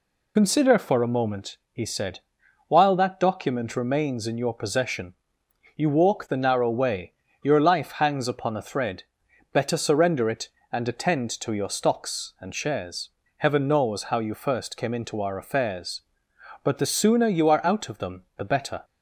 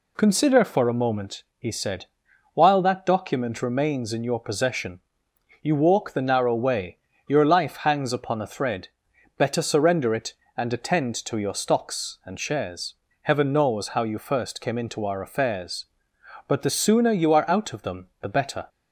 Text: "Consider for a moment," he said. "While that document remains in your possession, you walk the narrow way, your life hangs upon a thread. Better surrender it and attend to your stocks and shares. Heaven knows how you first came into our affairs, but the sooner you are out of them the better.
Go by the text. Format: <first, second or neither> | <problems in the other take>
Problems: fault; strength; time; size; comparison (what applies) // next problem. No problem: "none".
second | loses the start of "Consider"; at 0.3 s; 40 ms